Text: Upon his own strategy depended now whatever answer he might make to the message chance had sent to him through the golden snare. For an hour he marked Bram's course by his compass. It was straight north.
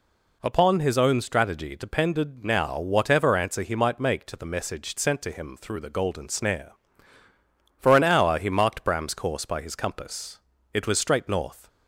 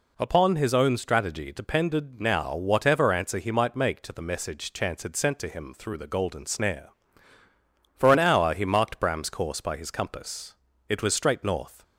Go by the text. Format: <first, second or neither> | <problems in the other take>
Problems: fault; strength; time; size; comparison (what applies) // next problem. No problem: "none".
second | skips "chance had"; at 4.9 s